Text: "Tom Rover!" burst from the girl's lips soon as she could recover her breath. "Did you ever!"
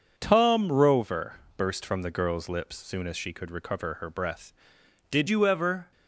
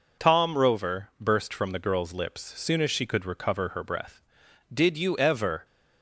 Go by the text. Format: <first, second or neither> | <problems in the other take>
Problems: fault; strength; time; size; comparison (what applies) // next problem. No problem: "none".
second | changes voice at "you"; from 5.2 s on; 0.7 s long